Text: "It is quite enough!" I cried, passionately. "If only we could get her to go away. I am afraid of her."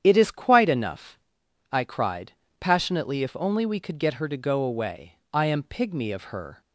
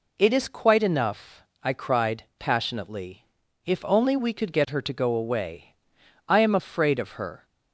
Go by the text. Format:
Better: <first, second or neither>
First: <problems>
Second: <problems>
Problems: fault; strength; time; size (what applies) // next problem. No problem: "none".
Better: second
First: starts louder than the rest; strong; until 1.0 s; 9 dB // says "pygmy" for "afraid"; at 5.6 s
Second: none